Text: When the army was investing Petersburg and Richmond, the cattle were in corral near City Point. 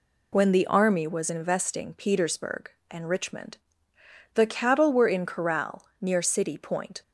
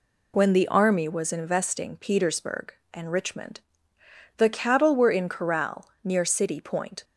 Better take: neither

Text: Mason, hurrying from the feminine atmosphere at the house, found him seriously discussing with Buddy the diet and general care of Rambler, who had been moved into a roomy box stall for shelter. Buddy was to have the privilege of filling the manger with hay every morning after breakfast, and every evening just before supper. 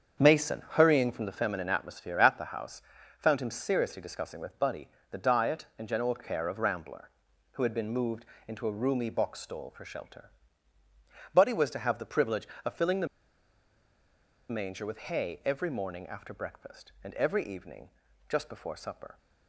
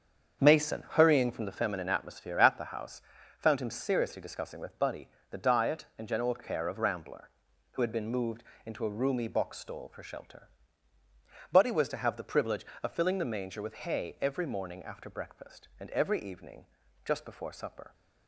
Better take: second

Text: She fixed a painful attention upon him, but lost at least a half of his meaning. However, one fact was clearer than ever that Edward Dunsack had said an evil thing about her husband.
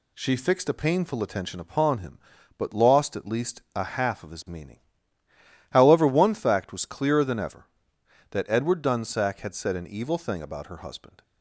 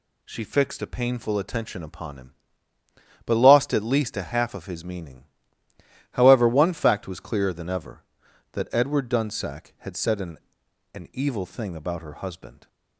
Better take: first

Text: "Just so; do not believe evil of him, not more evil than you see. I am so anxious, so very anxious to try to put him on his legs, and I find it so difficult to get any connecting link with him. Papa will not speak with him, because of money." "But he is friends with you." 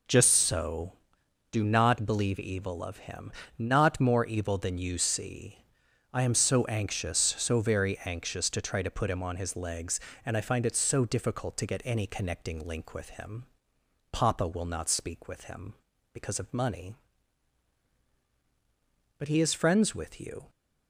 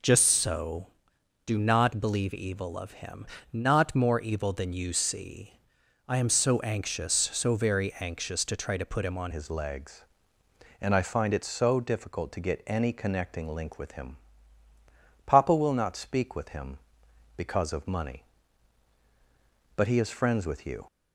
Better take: first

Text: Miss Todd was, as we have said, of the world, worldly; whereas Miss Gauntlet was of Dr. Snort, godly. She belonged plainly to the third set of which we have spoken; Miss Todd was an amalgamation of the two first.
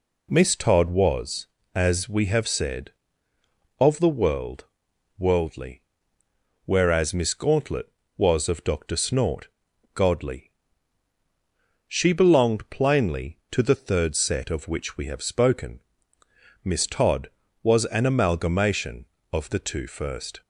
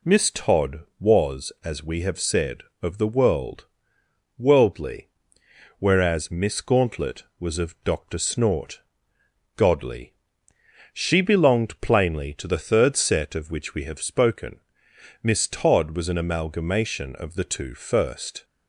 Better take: neither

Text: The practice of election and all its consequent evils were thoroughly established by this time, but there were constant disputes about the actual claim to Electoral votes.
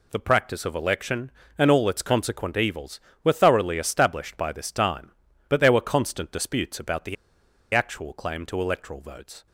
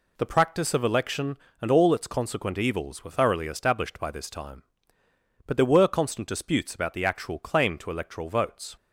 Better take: second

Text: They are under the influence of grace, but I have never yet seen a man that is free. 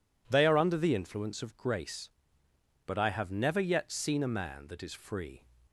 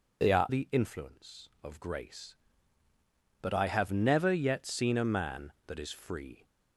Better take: first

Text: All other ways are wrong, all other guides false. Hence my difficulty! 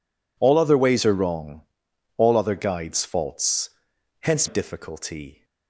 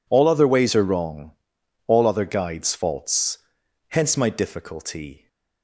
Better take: second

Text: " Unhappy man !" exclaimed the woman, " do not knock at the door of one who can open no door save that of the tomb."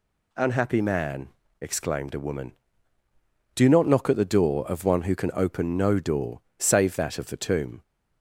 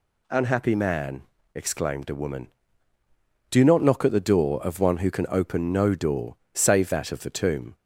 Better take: neither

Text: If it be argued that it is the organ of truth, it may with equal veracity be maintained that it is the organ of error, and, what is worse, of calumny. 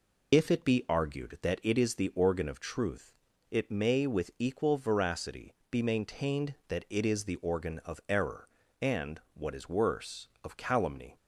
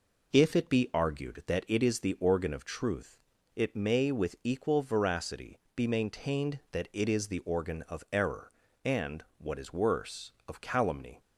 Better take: second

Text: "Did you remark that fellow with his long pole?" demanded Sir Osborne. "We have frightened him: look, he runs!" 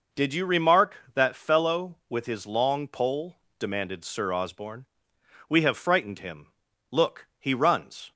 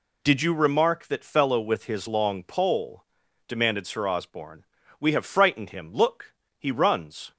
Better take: neither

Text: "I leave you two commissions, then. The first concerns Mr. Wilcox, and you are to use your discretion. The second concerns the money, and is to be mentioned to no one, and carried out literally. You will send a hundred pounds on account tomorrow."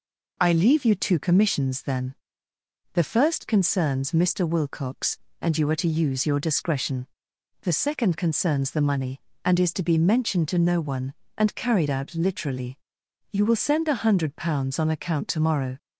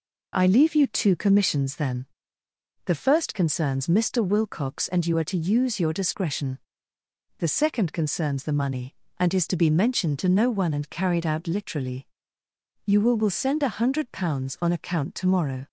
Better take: first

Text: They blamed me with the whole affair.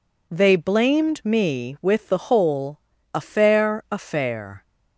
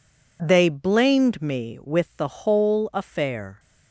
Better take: second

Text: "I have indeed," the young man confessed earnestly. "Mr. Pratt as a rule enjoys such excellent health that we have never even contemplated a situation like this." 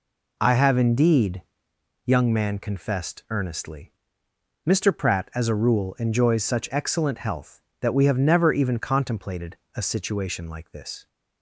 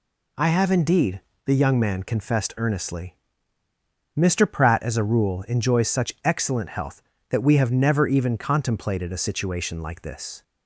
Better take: second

